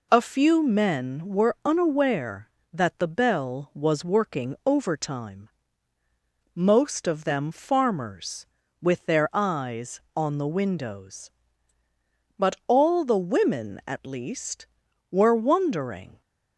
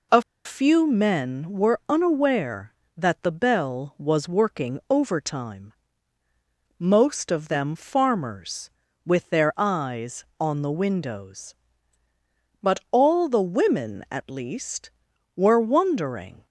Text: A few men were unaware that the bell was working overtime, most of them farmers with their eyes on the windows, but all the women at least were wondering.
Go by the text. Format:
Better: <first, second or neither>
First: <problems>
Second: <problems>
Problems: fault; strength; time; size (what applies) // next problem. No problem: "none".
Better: first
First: none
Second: pauses between "A" and "few"; slight; at 0.2 s; 0.22 s long